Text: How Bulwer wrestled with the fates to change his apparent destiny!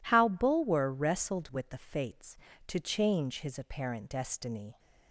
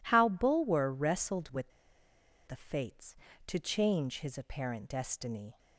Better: first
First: none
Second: pauses between "with" and "the"; noticeable; at 1.7 s; 0.77 s long

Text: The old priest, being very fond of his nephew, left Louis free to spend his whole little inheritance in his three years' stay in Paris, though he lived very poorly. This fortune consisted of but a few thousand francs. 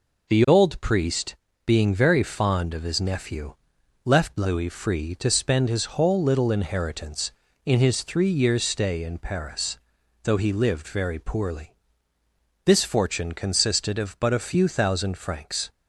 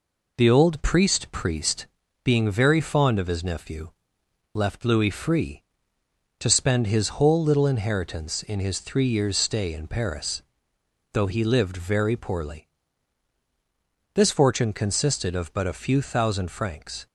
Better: first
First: none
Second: says "priest" twice; at 1.2 s

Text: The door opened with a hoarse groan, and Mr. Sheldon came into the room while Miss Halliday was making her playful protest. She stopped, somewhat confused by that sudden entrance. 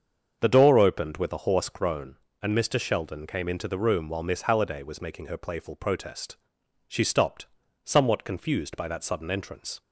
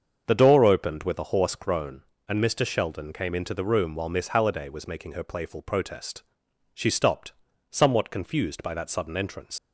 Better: first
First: starts louder than the rest; until 1.4 s; 7 dB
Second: starts louder than the rest; until 1.2 s; 7 dB // leaves "entrance" unfinished; at 9.5 s; 90 ms

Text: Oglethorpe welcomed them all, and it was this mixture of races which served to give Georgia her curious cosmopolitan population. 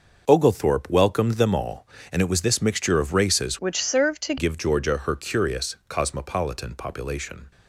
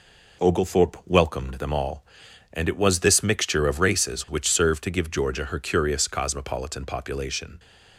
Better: second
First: changes voice from "which" to "to"; from 3.5 to 4.3 s; 0.8 s long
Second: none

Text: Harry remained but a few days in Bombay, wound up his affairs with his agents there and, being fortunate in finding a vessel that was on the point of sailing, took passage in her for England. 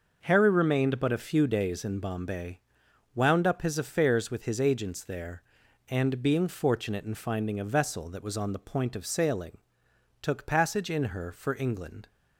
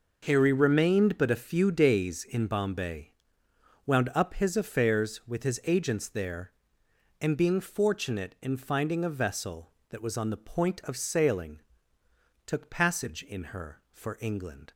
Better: neither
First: none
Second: none

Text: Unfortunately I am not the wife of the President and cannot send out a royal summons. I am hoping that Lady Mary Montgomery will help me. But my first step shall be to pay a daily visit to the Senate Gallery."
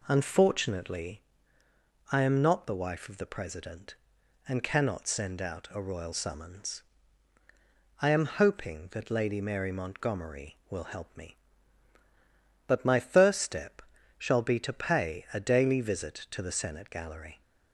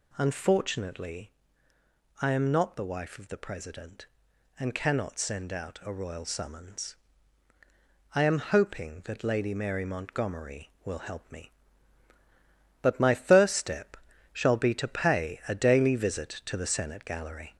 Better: first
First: pauses between "Unfortunately" and "I"; noticeable; at 1.2 s; 0.90 s long // pauses between "step" and "shall"; slight; at 13.8 s; 0.36 s long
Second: gets louder; slight; throughout; 2.5 dB // pauses between "Unfortunately" and "I"; noticeable; at 1.3 s; 0.90 s long // pauses between "step" and "shall"; slight; at 13.9 s; 0.36 s long

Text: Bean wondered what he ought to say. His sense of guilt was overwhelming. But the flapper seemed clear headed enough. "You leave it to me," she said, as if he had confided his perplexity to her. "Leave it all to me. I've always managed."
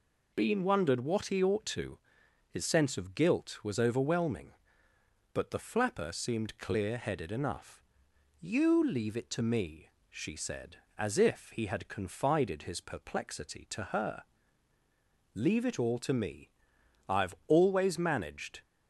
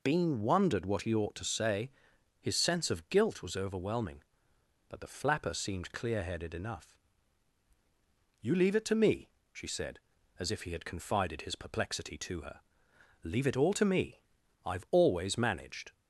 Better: second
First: skips "say"; at 2.2 s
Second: none

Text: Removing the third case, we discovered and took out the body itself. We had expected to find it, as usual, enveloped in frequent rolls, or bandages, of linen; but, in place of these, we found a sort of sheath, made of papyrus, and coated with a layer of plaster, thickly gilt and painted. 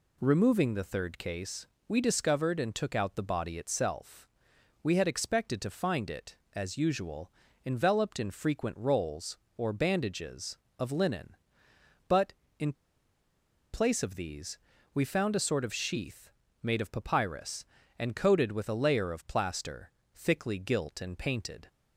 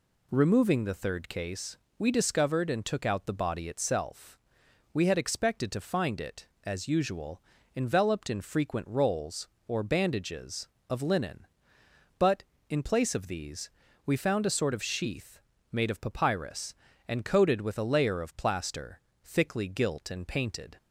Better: second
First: pauses between "in" and "place"; at 12.7 s; 1.0 s long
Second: none

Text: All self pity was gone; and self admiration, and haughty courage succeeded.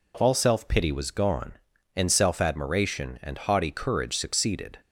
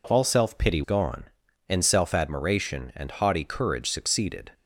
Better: first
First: none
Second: skips "was"; at 0.8 s

